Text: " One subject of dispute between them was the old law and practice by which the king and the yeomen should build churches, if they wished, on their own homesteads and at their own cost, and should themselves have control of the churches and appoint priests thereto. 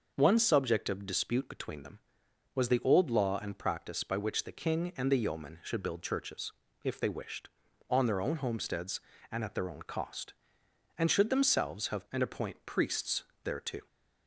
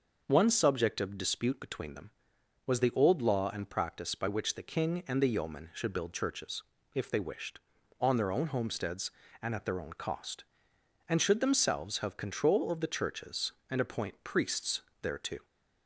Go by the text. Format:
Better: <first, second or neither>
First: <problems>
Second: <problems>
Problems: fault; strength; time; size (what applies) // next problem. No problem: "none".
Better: second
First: starts louder than the rest; noticeable; until 1.1 s; 6 dB // skips "control of the churches"; at 12.0 s // pauses between "priests" and "thereto"; slight; at 13.2 s; 0.22 s long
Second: starts louder than the rest; noticeable; until 1.2 s; 6 dB // pauses between "priests" and "thereto"; slight; at 14.8 s; 0.22 s long